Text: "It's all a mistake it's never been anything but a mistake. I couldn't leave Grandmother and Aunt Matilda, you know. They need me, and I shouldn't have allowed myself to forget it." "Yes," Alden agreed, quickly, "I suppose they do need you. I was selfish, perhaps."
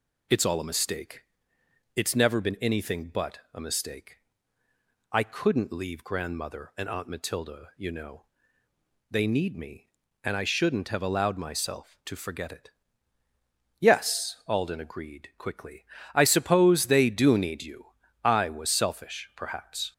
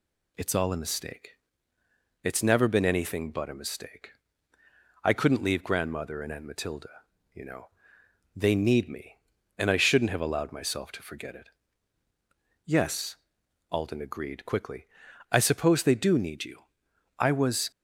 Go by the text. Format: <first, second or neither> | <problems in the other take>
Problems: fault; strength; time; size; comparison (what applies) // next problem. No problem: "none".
first | pauses between "mistake" and "it's"; noticeable; at 1.3 s; 0.86 s long; noticeable in the first // stops before "selfish perhaps"; at 17.7 s